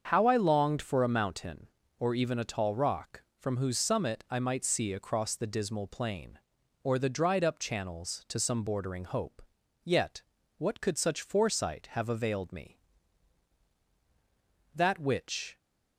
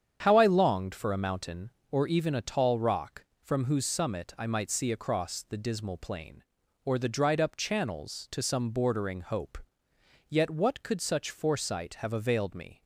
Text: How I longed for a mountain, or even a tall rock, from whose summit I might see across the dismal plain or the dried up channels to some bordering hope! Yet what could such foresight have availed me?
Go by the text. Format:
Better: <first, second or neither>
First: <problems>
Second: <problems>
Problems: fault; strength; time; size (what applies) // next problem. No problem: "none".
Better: second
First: starts louder than the rest; until 1.1 s; 7 dB // pauses between "Yet" and "what"; slight; at 10.2 s; 0.36 s long // goes on to say "That which"; noticeable; from 14.7 s on; 0.86 s long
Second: starts louder than the rest; strong; until 1.2 s; 8 dB